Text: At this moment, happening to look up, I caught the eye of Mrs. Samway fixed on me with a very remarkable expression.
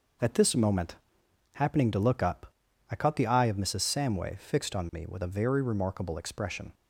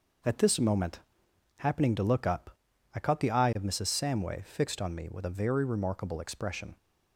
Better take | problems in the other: neither | none

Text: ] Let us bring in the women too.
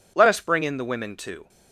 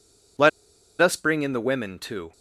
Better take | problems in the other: first | pauses between "Let" and "us"; noticeable; at 0.4 s; 0.51 s long

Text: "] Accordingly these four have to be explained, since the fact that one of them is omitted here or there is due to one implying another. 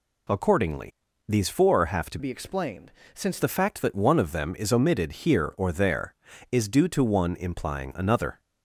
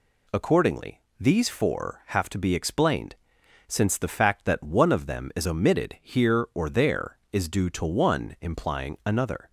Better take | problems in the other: second | pauses between "Accordingly" and "these"; slight; at 0.9 s; 0.34 s long; slight in the second // changes voice from "be" to "since"; from 2.1 to 3.3 s; 1.2 s long

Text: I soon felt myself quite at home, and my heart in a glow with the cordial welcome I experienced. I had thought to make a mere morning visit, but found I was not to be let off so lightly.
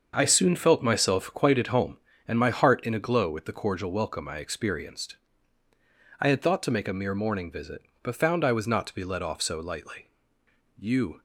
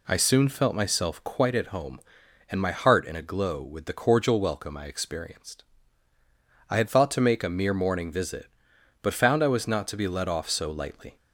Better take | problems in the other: second | starts louder than the rest; until 1.1 s; 6.5 dB // goes on to say "You"; slight; from 10.7 s on; 0.42 s long

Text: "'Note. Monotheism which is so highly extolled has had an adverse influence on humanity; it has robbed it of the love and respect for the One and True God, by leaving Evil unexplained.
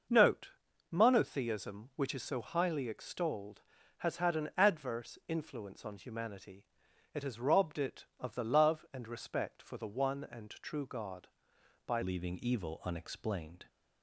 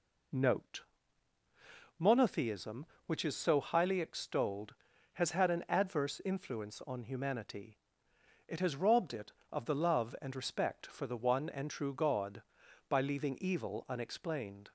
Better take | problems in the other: second | changes voice at "leaving"; from 12.0 s on; 1.6 s long

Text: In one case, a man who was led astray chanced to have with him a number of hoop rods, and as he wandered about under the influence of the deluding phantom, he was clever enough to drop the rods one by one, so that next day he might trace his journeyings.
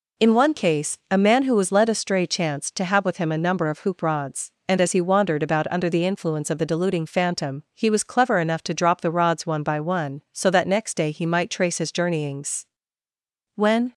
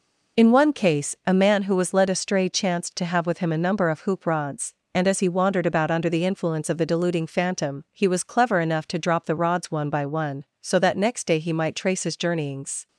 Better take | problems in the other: second | goes on to say "When"; slight; from 13.5 s on; 0.38 s long

